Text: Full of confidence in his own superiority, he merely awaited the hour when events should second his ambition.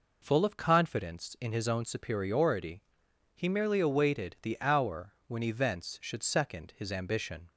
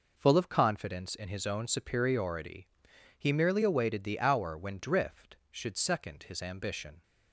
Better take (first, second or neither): first